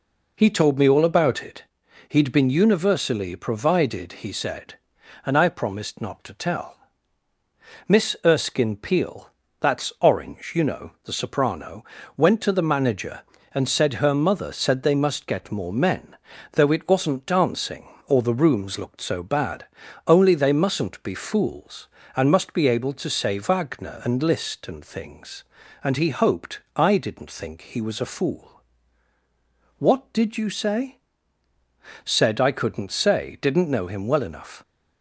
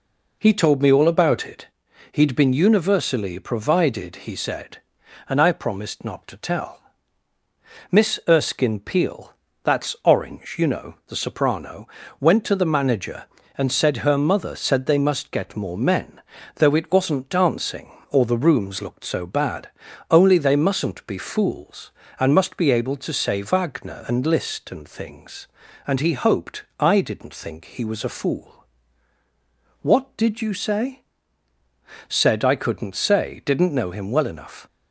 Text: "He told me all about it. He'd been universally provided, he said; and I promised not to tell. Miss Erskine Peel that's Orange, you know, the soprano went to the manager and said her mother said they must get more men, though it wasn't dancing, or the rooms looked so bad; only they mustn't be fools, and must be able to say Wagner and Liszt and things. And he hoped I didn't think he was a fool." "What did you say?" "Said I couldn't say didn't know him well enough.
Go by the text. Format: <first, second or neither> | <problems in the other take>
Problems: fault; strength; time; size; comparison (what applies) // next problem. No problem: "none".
neither | pauses between "Peel" and "that's"; slight; the same in both // pauses between "soprano" and "went"; slight; the same in both // pauses between "hoped" and "I"; slight; the same in both